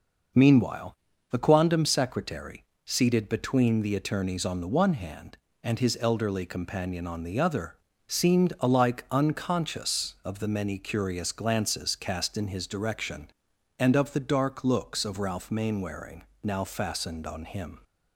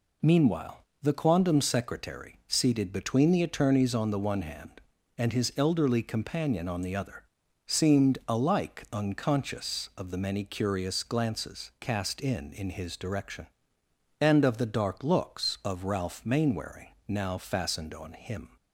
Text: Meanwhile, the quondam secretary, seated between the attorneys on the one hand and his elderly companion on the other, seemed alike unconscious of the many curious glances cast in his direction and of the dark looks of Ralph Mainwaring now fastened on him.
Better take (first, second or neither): first